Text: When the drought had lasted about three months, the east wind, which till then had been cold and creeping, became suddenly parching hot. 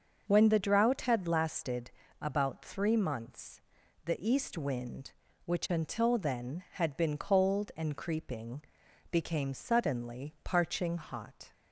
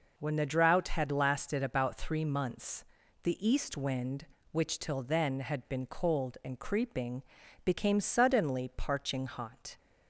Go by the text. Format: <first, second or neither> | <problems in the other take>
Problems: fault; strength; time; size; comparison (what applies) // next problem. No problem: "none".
second | starts louder than the rest; noticeable; until 1.2 s; 6 dB // pauses between "lasted" and "about"; slight; at 1.9 s; 0.28 s long // says "until" for "till"; at 5.7 s